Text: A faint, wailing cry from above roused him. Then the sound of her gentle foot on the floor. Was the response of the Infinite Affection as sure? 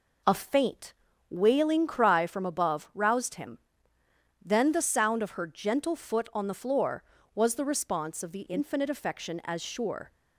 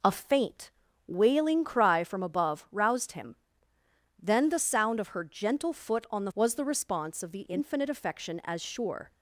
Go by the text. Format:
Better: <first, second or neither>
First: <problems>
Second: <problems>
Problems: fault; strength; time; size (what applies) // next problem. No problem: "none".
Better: first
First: none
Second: skips "floor"; at 6.3 s